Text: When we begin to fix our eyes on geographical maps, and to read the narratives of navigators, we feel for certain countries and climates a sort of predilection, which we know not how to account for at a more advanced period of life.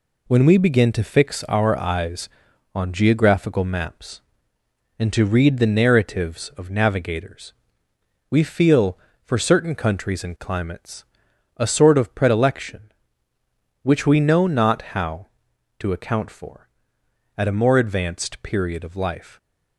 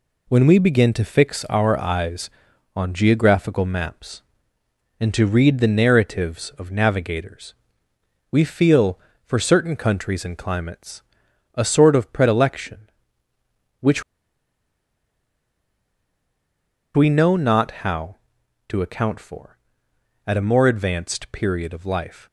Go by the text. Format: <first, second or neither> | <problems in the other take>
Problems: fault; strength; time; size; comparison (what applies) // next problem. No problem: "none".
first | pauses between "climates" and "a"; noticeable; at 11.0 s; 0.54 s long; noticeable in the first // pauses between "which" and "we"; strong; at 14.0 s; 2.9 s long